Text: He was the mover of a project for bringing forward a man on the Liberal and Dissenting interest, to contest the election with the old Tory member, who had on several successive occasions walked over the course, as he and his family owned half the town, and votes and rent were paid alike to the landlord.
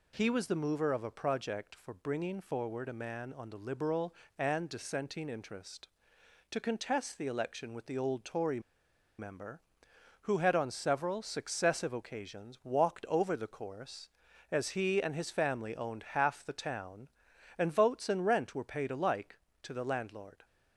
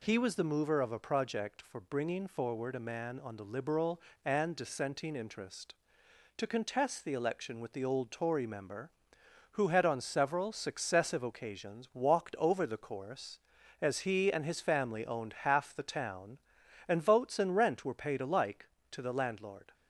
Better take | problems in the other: second | pauses between "Tory" and "member"; noticeable; at 8.6 s; 0.58 s long

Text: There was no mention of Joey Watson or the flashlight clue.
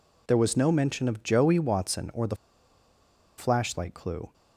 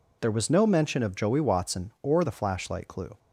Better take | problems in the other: second | pauses between "the" and "flashlight"; at 2.3 s; 1.0 s long

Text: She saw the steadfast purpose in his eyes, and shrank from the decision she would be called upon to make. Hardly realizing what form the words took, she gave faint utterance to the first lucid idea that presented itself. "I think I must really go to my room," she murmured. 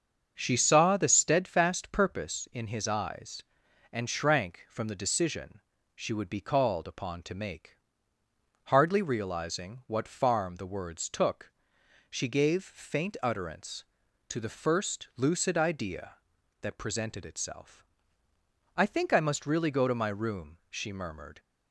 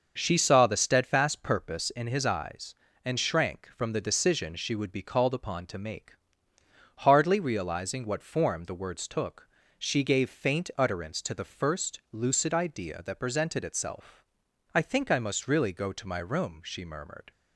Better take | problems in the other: second | starts louder than the rest; until 1.3 s; 7 dB; also in the second // pauses between "decision" and "she"; slight; at 5.6 s; 0.34 s long // says "farm" for "form"; at 10.0 s

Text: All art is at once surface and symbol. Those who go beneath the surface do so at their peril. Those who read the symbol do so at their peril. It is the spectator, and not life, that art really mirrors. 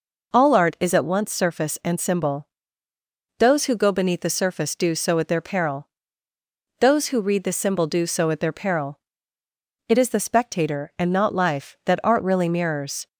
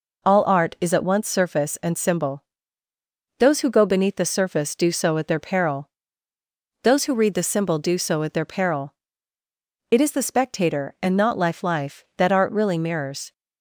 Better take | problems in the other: first | says "life" twice; at 11.6 s

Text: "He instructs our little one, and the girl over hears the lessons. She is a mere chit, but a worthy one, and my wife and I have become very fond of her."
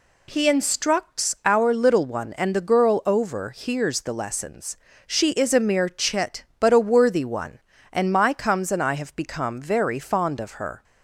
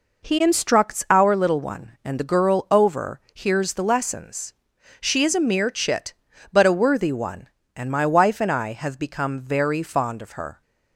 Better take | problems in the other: second | says "comes" for "wife"; at 8.3 s

